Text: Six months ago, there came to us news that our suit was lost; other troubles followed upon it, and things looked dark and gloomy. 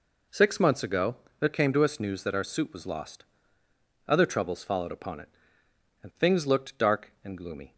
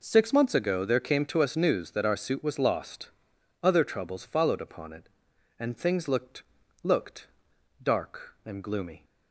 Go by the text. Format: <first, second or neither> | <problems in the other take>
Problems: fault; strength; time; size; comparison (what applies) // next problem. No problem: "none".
first | says "looked" twice; at 6.8 s